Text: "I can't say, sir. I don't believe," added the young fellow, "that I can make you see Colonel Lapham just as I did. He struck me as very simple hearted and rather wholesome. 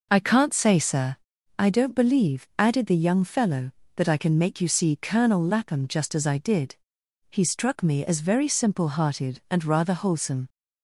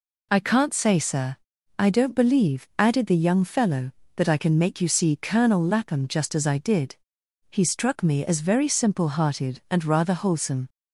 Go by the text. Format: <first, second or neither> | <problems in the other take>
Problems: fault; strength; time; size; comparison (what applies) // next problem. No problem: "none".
second | starts louder than the rest; noticeable; until 1.6 s; 5 dB